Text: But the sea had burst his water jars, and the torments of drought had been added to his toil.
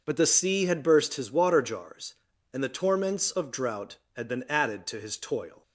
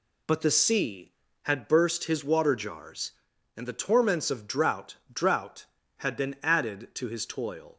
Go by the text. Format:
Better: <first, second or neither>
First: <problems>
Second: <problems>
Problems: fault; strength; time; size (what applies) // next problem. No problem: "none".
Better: first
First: none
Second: says "drought" twice; at 5.1 s